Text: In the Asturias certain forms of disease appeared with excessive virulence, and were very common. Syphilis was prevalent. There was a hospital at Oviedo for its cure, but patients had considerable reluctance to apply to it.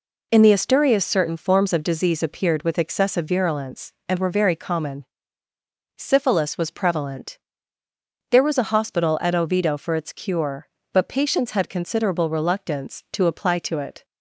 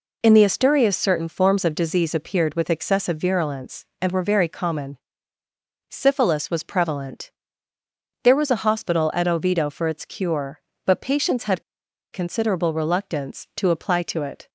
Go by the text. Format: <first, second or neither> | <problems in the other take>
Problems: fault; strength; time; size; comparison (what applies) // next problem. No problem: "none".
first | pauses between "had" and "considerable"; noticeable; at 11.6 s; 0.49 s long